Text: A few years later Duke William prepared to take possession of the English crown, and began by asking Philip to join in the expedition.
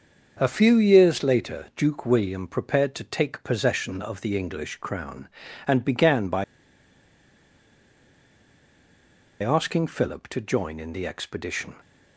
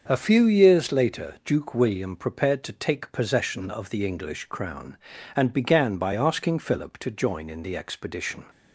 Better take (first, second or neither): second